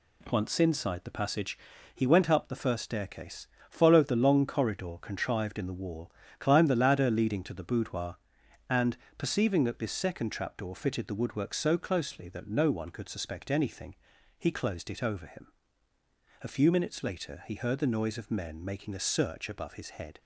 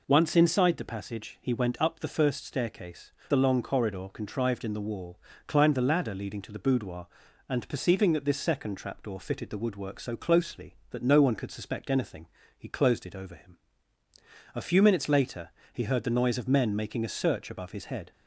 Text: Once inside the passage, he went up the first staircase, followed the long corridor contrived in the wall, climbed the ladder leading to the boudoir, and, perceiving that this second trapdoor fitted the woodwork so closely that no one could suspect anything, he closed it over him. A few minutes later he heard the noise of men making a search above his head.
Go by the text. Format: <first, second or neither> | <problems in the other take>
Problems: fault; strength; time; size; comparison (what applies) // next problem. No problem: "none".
first | skips "followed"; at 3.2 s // pauses between "later" and "he"; slight; at 15.4 s; 0.24 s long